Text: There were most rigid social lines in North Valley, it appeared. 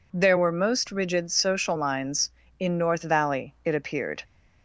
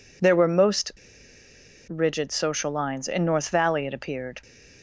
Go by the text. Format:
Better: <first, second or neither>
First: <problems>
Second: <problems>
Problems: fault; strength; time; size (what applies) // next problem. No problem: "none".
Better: first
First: none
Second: pauses between "most" and "rigid"; noticeable; at 0.9 s; 0.96 s long